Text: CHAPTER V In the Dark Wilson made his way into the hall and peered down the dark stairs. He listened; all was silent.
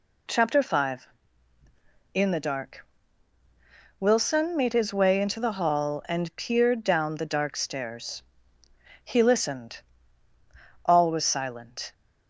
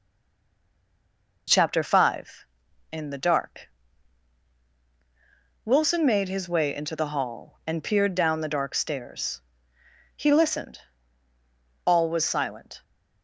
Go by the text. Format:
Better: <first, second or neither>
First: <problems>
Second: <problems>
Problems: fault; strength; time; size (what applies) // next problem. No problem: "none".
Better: first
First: pauses between "Dark" and "Wilson"; at 2.8 s; 1.1 s long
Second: stays silent before the first word; noticeable; until 1.4 s; 1.4 s long // pauses between "Dark" and "Wilson"; strong; at 3.7 s; 1.9 s long